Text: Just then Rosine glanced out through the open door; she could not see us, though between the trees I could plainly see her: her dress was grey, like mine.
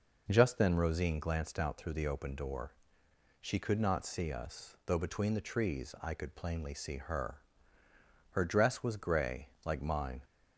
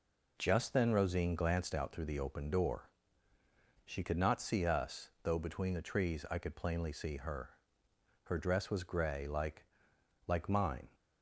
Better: first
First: none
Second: says "like" twice; at 10.2 s

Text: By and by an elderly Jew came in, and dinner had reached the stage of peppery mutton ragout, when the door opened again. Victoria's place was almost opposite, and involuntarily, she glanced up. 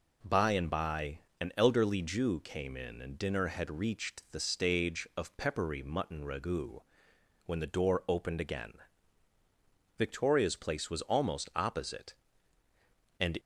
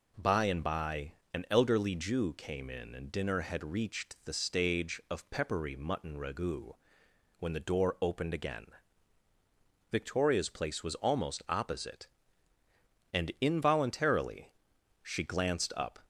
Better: second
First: pauses between "by" and "an"; slight; at 1.1 s; 0.22 s long // stops before "involuntarily she glanced up"; at 13.3 s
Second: pauses between "by" and "an"; slight; at 1.1 s; 0.22 s long

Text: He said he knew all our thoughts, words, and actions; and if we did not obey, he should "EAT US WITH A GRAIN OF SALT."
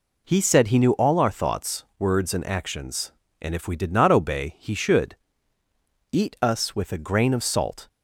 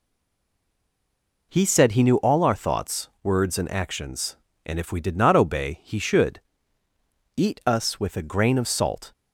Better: first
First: pauses between "should" and "EAT"; noticeable; at 5.1 s; 0.96 s long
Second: stays silent before the first word; noticeable; until 1.5 s; 1.5 s long // pauses between "should" and "EAT"; noticeable; at 6.4 s; 0.96 s long

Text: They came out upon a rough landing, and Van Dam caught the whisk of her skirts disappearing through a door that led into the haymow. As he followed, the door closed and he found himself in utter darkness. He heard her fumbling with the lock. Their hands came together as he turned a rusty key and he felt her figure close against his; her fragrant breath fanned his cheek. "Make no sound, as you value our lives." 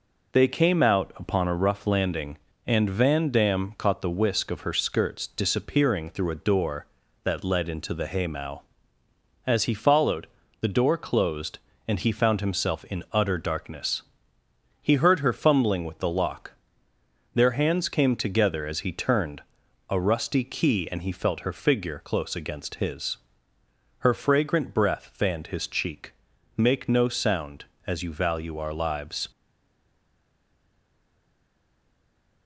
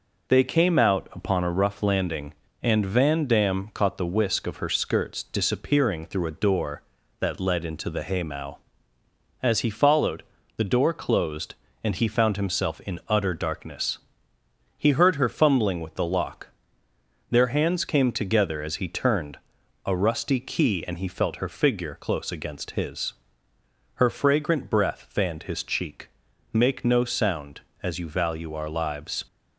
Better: second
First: pauses between "turned" and "a"; noticeable; at 19.4 s; 0.48 s long // stays silent after the last word; strong; from 29.3 s on; 3.1 s long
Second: pauses between "turned" and "a"; noticeable; at 19.3 s; 0.48 s long

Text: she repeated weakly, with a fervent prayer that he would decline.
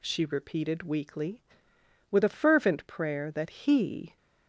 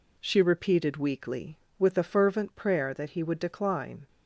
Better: second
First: stops before "would decline"; at 4.1 s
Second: none

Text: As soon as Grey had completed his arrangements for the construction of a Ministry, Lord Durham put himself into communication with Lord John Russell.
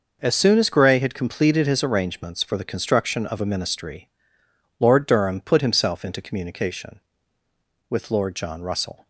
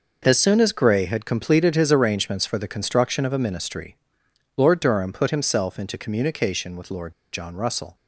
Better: first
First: none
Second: pauses between "Lord" and "John"; slight; at 7.1 s; 0.21 s long

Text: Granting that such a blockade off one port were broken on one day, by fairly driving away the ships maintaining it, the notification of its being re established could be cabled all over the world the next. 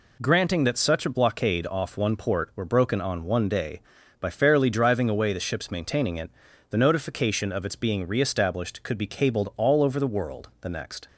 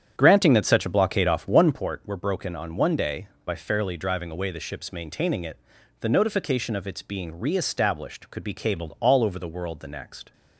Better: first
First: none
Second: starts louder than the rest; strong; until 1.9 s; 9 dB

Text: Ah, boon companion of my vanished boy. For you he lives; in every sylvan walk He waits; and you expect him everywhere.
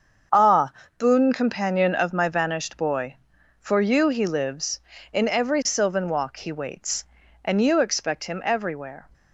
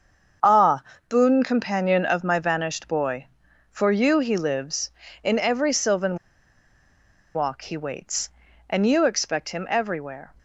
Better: first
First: starts louder than the rest; until 1.6 s; 7 dB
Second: starts louder than the rest; until 1.7 s; 7 dB // pauses between "sylvan" and "walk"; at 6.1 s; 1.1 s long

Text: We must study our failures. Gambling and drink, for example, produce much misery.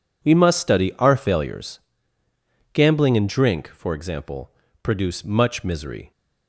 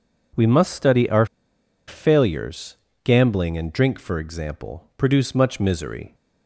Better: first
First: none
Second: pauses between "our" and "failures"; noticeable; at 1.2 s; 0.61 s long

